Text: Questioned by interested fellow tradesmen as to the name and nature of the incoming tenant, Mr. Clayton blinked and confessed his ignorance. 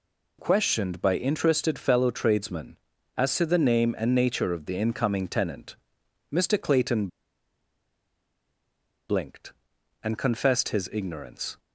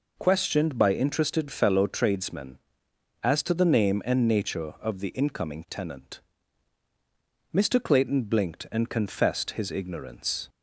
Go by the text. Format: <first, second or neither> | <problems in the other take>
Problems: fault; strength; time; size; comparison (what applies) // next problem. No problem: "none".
second | pauses between "Clayton" and "blinked"; strong; at 7.0 s; 2.0 s long